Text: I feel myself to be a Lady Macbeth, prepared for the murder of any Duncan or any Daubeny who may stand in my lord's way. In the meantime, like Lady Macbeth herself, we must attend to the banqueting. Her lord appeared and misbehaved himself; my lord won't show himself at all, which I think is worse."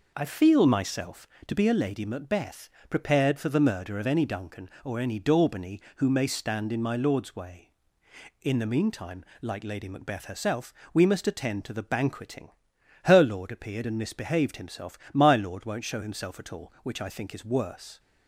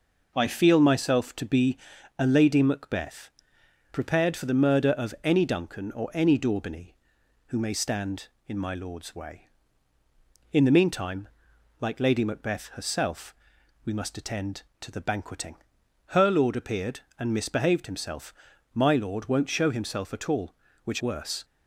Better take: first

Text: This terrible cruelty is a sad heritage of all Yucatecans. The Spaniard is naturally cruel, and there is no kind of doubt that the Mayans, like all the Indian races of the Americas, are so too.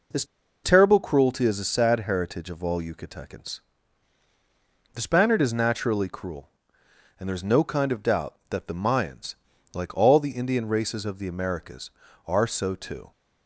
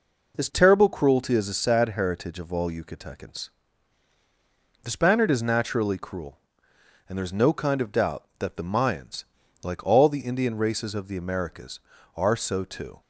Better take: second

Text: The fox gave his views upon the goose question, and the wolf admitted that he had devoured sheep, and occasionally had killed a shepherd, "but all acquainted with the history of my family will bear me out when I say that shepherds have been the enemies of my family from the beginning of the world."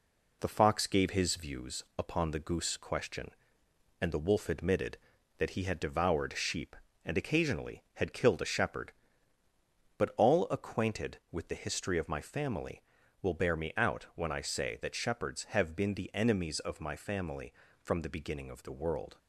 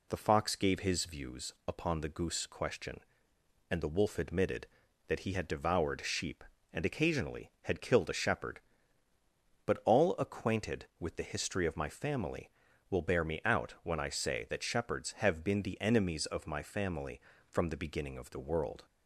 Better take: second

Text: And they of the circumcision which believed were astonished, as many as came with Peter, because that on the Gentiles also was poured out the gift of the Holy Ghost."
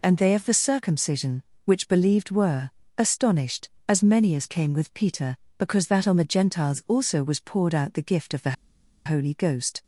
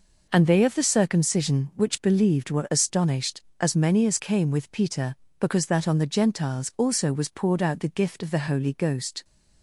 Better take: second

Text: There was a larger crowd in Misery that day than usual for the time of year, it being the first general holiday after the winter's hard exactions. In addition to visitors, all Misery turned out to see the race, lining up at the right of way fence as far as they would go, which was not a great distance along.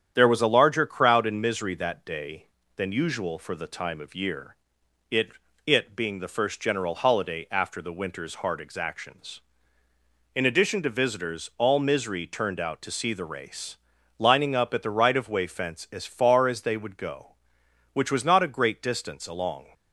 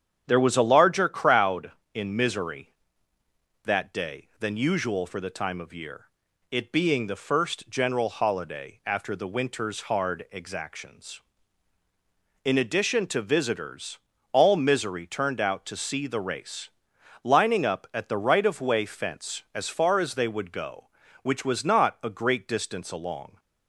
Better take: second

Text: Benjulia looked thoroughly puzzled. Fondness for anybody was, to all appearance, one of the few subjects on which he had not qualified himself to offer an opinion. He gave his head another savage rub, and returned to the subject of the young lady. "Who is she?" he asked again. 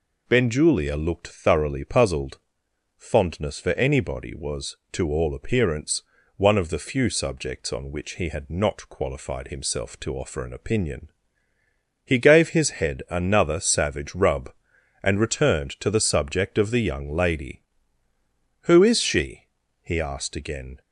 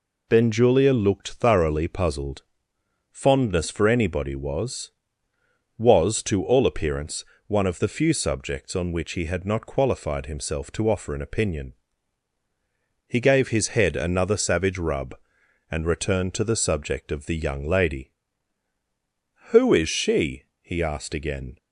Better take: first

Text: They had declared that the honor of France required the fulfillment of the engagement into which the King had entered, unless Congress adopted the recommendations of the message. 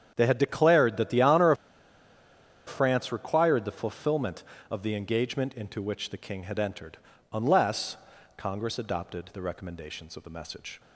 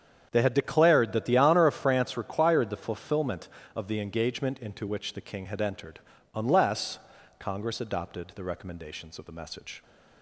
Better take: second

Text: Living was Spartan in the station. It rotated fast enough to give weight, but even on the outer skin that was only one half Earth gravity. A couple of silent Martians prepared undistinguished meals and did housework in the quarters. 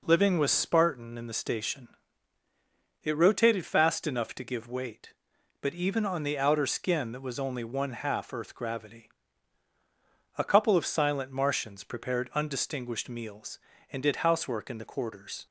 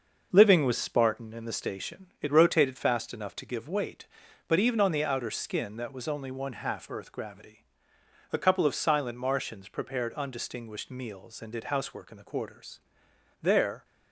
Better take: first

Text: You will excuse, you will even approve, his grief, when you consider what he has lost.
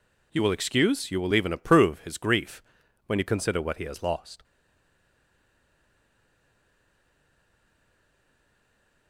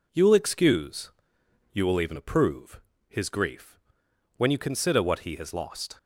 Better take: second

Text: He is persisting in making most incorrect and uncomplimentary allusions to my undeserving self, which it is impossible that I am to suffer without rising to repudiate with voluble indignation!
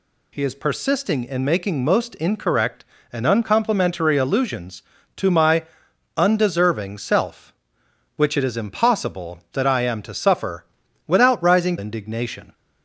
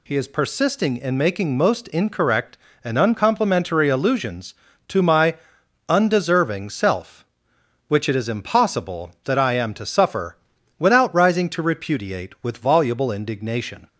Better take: second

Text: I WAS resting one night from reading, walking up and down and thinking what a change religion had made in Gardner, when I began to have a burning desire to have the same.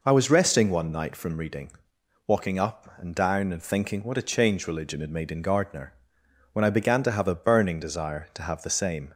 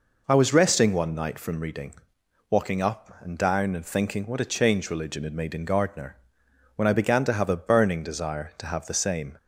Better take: neither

